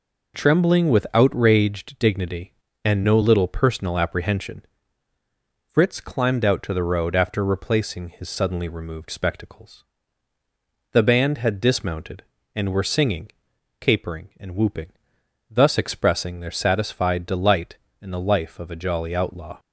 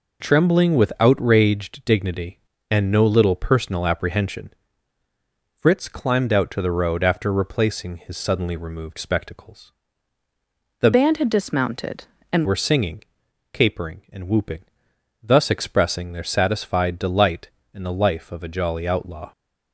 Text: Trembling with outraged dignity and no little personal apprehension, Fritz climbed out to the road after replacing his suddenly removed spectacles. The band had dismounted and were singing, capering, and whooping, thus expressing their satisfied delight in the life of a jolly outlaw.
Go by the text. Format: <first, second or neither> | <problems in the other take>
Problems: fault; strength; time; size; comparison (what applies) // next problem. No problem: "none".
first | changes voice from "band" to "and"; from 10.9 to 12.4 s; 1.5 s long